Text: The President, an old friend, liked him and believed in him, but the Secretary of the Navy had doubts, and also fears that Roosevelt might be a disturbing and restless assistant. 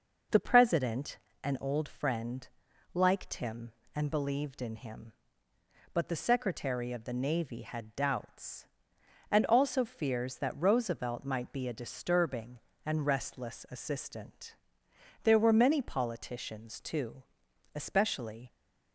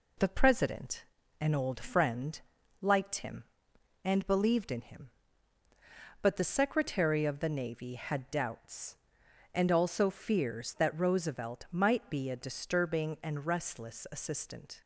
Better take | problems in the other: second | goes on to say "There were many politicians too especially"; strong; from 15.2 s on; 3.2 s long

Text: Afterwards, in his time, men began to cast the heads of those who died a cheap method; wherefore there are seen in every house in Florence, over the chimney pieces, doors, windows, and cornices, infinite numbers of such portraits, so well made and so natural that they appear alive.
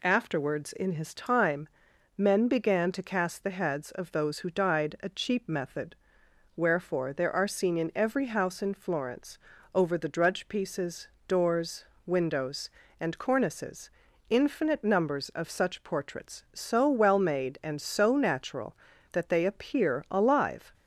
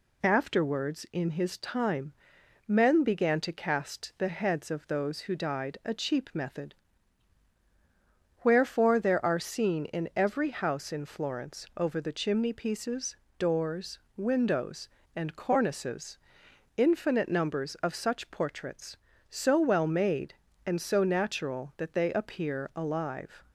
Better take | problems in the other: second | says "drudge" for "chimney"; at 10.0 s

